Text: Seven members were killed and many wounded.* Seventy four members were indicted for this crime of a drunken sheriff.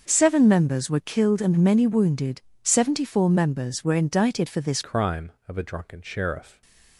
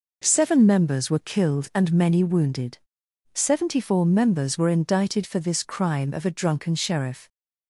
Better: second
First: starts louder than the rest; until 1.0 s; 6 dB // changes voice at "crime"; from 4.8 s on; 1.8 s long // stays silent after the last word; slight; from 6.4 s on; 0.5 s long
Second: none

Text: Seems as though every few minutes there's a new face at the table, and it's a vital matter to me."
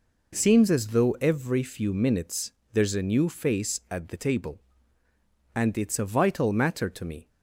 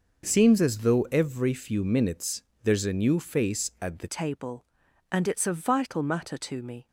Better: first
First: pauses between "minutes" and "there's"; slight; at 2.5 s; 0.18 s long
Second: pauses between "minutes" and "there's"; slight; at 2.4 s; 0.18 s long // changes voice at "table"; from 4.0 s on; 2.8 s long

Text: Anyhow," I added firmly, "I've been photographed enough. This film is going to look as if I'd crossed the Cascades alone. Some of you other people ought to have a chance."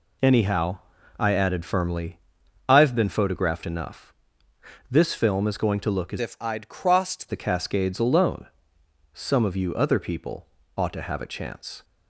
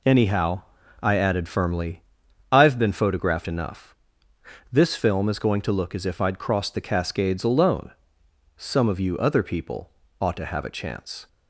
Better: second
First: changes voice from "if" to "crossed"; from 6.1 to 7.2 s; 1.1 s long // pauses between "people" and "ought"; slight; at 10.4 s; 0.30 s long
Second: pauses between "people" and "ought"; slight; at 9.8 s; 0.30 s long

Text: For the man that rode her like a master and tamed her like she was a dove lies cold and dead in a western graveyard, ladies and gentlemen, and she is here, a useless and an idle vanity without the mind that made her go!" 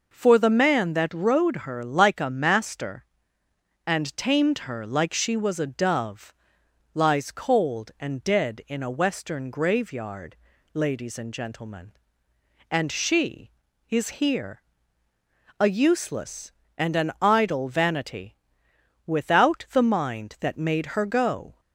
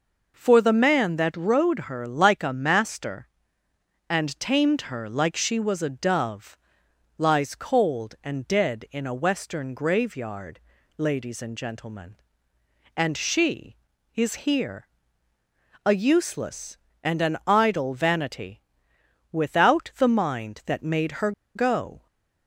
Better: first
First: pauses between "dove" and "lies"; noticeable; at 6.3 s; 0.62 s long // pauses between "vanity" and "without"; noticeable; at 18.3 s; 0.70 s long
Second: pauses between "dove" and "lies"; noticeable; at 6.5 s; 0.62 s long // pauses between "vanity" and "without"; noticeable; at 18.6 s; 0.70 s long // pauses between "her" and "go"; slight; at 21.3 s; 0.24 s long

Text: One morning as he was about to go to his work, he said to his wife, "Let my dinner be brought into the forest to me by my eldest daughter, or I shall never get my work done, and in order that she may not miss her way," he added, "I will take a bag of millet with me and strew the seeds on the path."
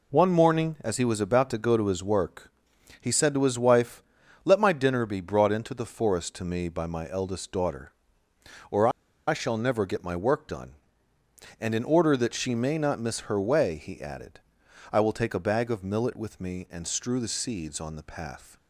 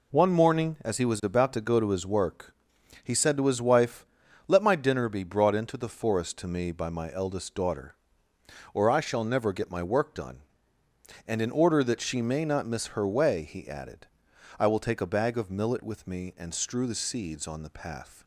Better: second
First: pauses between "or" and "I"; at 8.8 s; 0.38 s long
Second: none

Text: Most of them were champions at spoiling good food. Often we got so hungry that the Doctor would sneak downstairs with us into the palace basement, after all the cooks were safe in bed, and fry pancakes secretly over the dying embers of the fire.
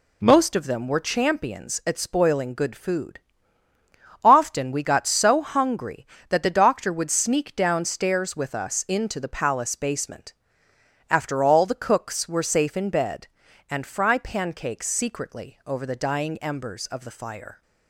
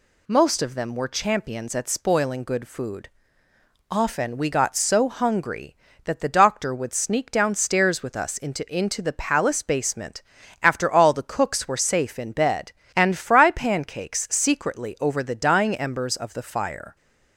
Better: first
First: none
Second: says "into" twice; at 8.7 s

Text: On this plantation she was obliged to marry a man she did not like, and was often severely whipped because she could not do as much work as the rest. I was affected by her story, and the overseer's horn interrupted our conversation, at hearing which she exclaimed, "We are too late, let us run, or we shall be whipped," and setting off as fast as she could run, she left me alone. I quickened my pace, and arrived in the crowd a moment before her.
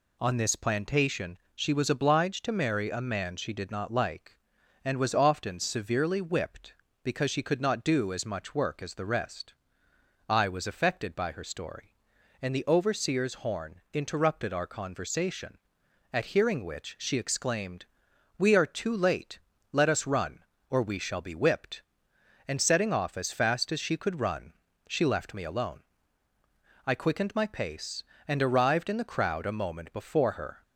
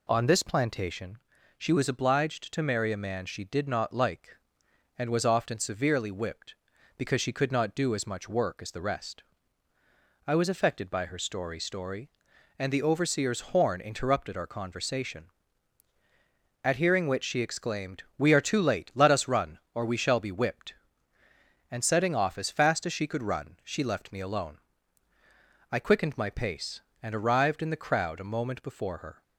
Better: first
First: pauses between "plantation" and "she"; slight; at 1.3 s; 0.16 s long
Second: pauses between "plantation" and "she"; at 1.1 s; 0.40 s long // says "story" twice; at 11.5 s

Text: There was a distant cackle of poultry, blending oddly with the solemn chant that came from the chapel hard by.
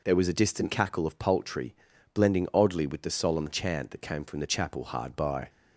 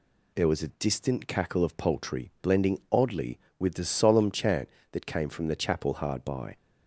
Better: neither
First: none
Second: none

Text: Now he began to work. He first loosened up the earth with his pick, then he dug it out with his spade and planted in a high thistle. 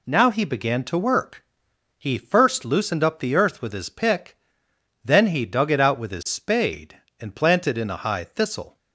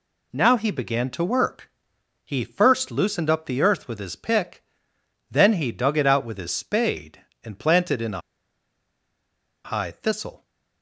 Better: first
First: none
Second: pauses between "a" and "high"; strong; at 8.2 s; 1.4 s long

